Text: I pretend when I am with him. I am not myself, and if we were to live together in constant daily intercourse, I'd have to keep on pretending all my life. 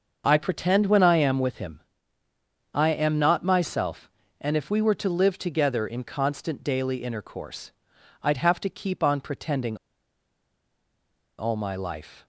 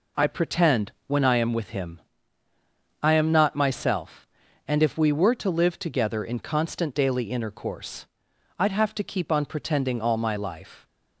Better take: second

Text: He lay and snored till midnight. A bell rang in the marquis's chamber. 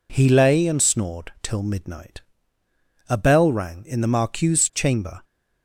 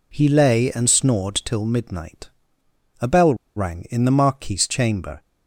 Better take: first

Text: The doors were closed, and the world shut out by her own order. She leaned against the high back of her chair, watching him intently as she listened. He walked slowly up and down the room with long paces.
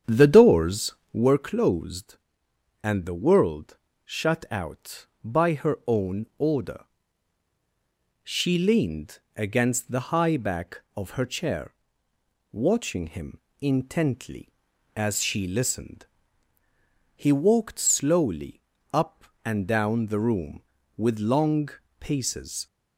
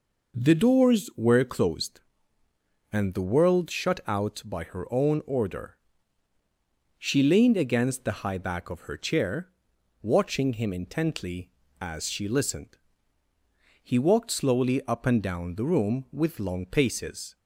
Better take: second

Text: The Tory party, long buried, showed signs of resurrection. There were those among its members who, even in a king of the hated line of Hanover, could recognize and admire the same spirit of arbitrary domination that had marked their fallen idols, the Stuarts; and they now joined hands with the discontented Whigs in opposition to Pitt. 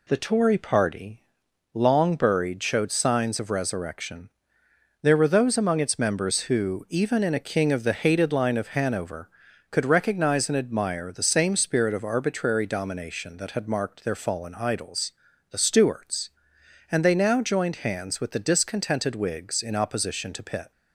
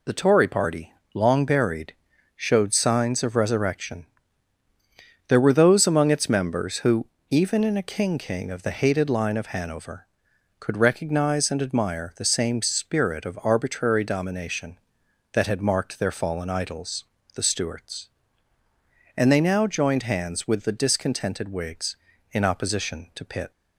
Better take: first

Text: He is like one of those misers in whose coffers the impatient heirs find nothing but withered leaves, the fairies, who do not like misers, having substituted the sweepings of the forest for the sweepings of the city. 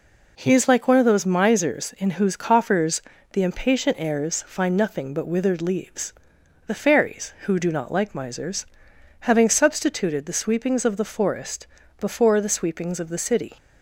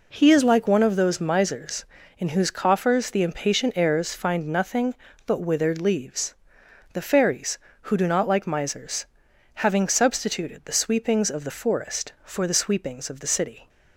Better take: second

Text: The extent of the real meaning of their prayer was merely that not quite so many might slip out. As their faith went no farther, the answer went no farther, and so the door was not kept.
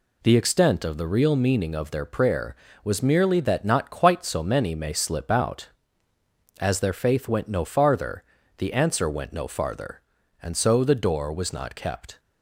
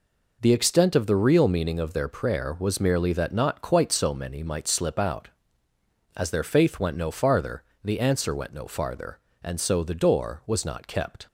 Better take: second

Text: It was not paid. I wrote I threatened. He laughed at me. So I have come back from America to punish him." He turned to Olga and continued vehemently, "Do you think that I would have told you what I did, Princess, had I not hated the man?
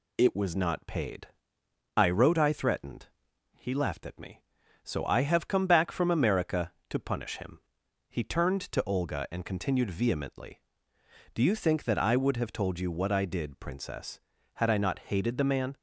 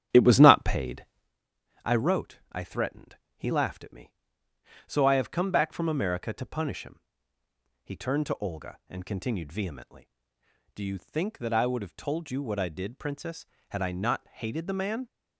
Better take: first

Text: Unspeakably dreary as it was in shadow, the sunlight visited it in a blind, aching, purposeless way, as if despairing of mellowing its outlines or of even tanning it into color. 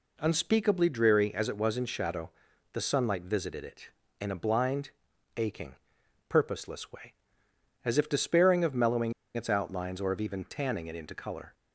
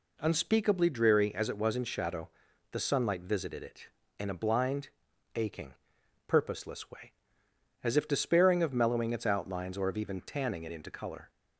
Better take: second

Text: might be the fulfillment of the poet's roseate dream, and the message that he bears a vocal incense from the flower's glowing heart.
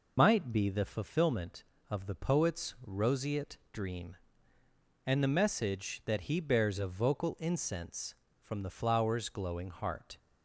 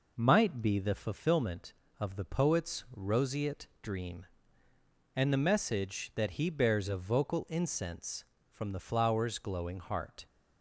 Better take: second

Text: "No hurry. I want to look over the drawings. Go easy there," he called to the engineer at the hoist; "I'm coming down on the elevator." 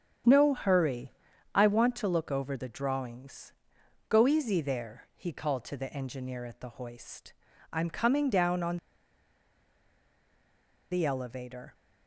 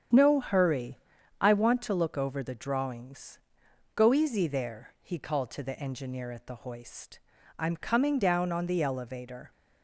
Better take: second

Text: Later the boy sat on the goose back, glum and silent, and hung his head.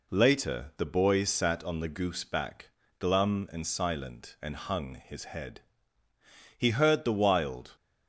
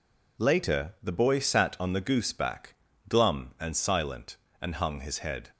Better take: second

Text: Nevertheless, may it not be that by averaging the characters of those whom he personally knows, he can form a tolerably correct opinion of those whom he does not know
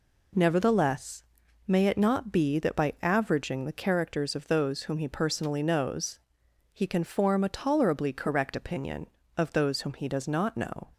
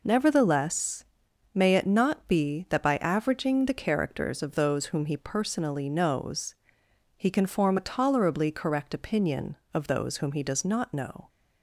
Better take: neither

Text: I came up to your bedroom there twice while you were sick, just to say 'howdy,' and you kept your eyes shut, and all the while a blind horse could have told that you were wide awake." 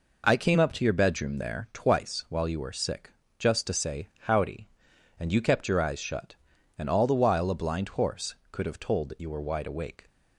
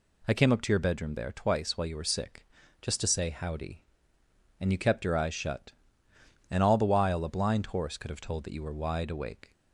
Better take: neither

